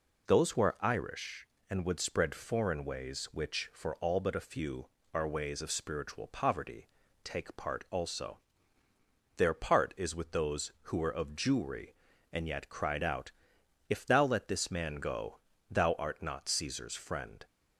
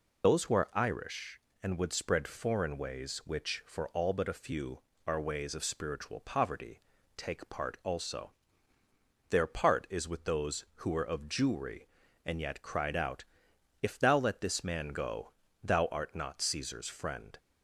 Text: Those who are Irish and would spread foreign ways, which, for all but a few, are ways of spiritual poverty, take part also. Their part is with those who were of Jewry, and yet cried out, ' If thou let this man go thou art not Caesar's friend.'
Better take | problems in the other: first | loses the start of "Those"; at 0.2 s; 45 ms // pauses between "go" and "thou"; slight; at 15.3 s; 0.32 s long; slight in the first

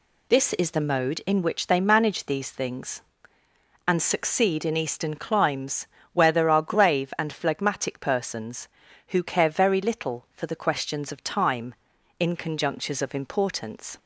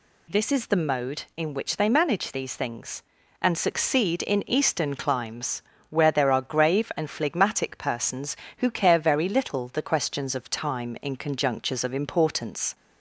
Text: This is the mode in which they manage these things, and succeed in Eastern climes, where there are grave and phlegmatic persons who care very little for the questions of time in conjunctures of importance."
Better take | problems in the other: first | skips "for"; at 9.6 s

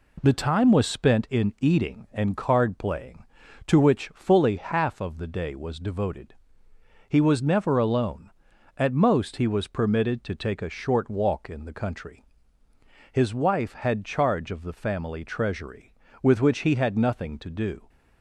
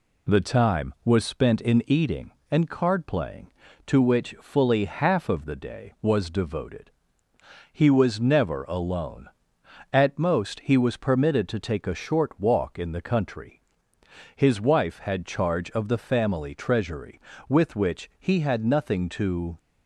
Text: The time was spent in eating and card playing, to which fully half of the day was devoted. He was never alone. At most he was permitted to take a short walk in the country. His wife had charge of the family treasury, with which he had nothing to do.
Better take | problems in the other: first | stops before "do"; at 19.5 s

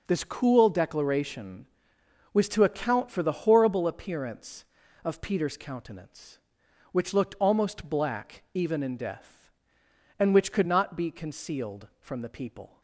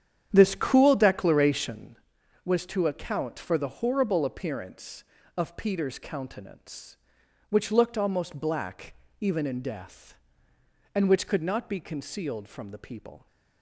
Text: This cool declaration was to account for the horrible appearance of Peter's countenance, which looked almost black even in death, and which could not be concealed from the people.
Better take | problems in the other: first | starts louder than the rest; strong; until 2.0 s; 9 dB // pauses between "black" and "even"; slight; at 8.9 s; 0.24 s long

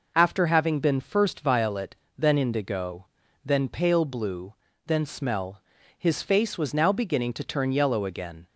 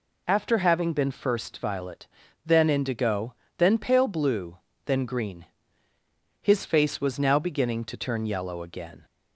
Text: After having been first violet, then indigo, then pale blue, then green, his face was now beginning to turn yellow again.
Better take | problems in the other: second | says "smell" for "green"; at 5.0 s

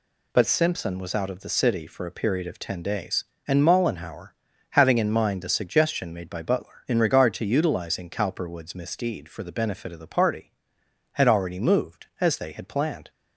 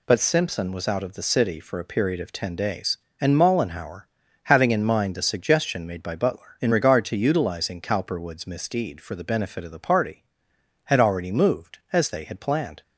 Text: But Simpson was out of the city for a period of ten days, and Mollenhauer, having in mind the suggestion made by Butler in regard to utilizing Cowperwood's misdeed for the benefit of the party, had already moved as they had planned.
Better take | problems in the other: neither | none

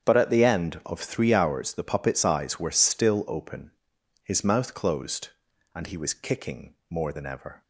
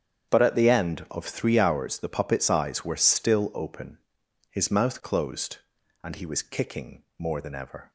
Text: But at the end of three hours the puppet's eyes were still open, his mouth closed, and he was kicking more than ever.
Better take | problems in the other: neither | starts louder than the rest; strong; the same in both // pauses between "kicking" and "more"; slight; the same in both

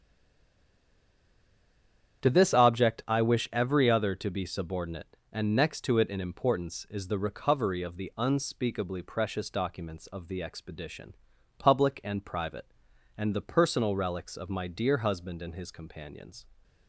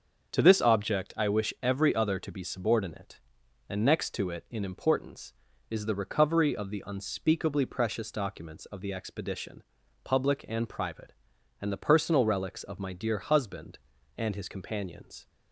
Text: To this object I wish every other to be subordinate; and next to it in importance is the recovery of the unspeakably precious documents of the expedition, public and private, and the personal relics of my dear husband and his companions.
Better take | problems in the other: second | stays silent before the first word; until 2.2 s; 2.2 s long // starts louder than the rest; strong; until 3.2 s; 8.5 dB; also in the second

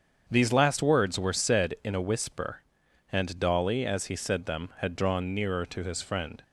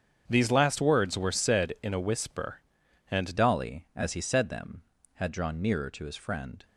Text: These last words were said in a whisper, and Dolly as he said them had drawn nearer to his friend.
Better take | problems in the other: first | starts louder than the rest; strong; until 1.2 s; 7.5 dB; strong in the first // changes voice at "Dolly"; from 3.3 s on; 3.3 s long

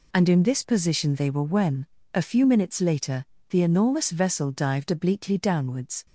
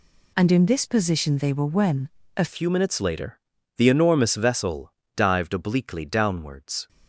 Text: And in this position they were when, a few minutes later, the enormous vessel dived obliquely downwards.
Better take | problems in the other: first | changes voice at "few"; from 2.4 s on; 4.4 s long // pauses between "vessel" and "dived"; slight; at 4.9 s; 0.24 s long

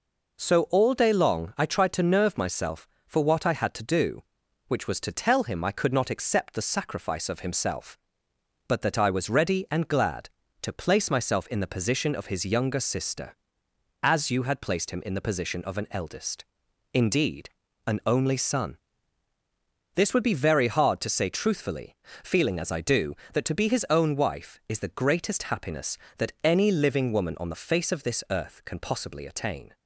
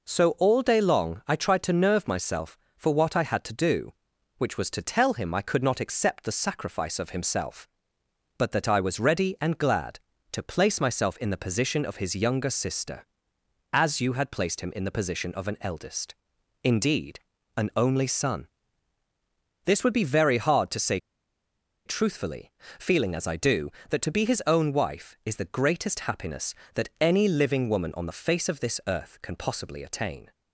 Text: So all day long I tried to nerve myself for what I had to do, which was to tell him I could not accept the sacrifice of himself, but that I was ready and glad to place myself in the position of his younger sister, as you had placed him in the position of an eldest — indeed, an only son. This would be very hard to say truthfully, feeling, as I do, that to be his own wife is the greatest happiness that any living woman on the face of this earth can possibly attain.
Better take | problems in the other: first | pauses between "say" and "truthfully"; noticeable; at 20.9 s; 0.88 s long

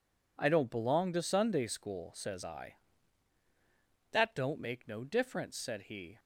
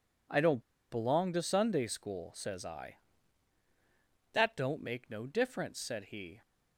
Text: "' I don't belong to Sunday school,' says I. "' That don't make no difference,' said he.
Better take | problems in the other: first | pauses between "don't" and "belong"; slight; at 0.6 s; 0.30 s long

